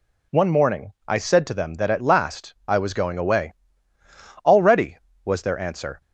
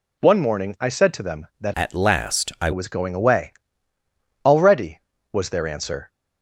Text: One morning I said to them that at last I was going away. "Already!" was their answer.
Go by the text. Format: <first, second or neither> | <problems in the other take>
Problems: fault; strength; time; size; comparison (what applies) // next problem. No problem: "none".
first | changes voice from "at" to "I"; from 1.7 to 2.7 s; 1.0 s long